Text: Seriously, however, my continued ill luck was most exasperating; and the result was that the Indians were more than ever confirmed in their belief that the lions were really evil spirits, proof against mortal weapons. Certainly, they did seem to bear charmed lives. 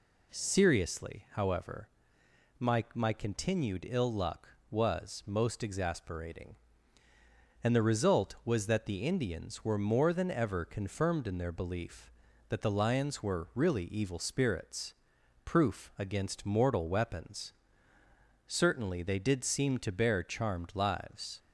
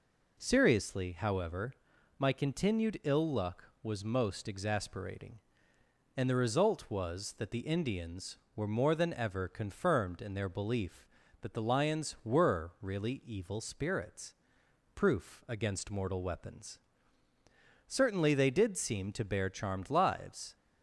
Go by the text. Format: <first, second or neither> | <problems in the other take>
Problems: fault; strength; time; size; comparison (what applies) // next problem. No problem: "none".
second | says "my" twice; at 2.9 s